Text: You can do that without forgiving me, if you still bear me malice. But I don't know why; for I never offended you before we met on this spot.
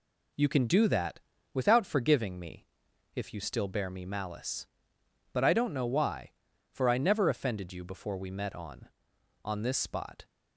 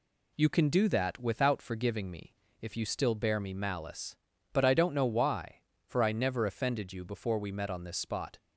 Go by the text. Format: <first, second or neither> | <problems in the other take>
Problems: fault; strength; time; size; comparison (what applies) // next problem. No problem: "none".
second | pauses between "that" and "without"; slight; at 1.1 s; 0.34 s long // says "on" twice; at 9.4 s